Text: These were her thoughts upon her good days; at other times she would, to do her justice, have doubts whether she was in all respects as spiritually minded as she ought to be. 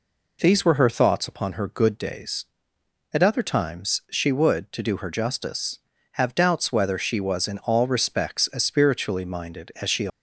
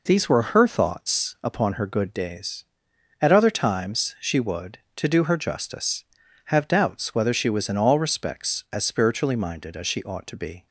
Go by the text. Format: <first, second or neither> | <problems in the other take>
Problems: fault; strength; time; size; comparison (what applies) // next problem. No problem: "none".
second | stops before "ought to be"; at 10.0 s